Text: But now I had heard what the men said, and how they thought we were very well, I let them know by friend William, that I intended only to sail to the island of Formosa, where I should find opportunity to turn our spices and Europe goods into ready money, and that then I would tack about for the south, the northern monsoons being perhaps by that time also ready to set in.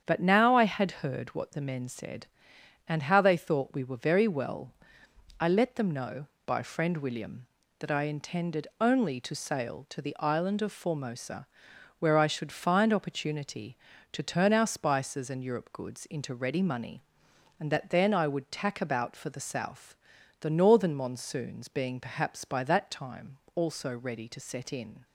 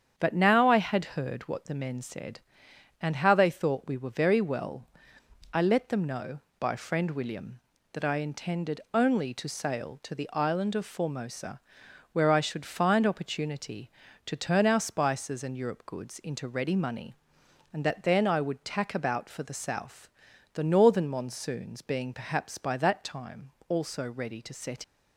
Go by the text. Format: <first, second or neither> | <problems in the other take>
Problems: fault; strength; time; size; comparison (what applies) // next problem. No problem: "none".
first | starts louder than the rest; strong; until 1.1 s; 8 dB; strong in the first // pauses between "time" and "also"; slight; at 23.5 s; 0.18 s long; slight in the first // stops before "in"; at 24.8 s